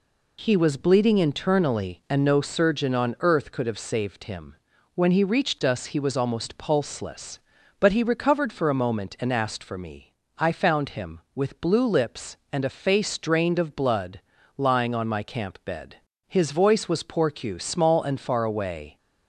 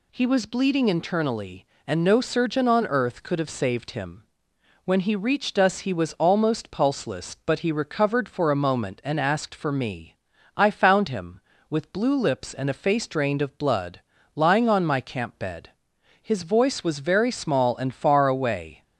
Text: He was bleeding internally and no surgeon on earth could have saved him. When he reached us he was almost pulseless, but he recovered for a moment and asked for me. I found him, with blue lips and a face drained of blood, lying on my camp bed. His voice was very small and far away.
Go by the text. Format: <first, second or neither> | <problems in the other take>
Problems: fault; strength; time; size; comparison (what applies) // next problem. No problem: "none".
second | says "porcu" for "very"; at 17.0 s